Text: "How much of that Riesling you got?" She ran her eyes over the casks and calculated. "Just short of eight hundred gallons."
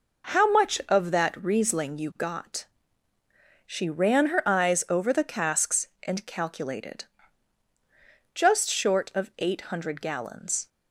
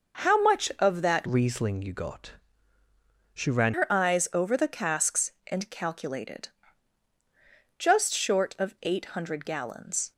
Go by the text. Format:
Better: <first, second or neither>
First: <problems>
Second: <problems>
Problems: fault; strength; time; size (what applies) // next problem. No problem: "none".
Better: first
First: none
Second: changes voice from "Riesling" to "ran"; from 1.2 to 3.7 s; 2.5 s long